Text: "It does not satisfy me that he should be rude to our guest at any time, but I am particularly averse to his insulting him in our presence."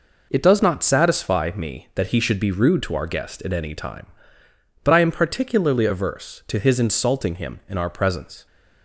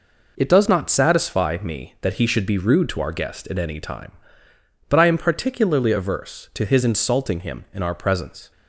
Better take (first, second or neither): neither